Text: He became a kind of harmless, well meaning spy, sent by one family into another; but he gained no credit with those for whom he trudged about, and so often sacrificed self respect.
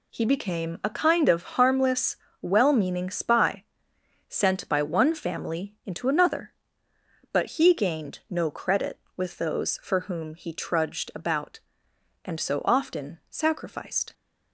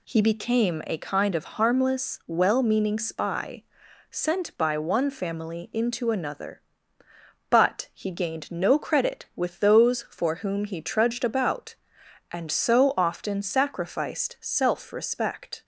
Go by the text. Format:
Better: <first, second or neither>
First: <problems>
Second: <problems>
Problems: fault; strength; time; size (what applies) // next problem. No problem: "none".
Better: second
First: stops before "self respect"; at 14.1 s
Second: none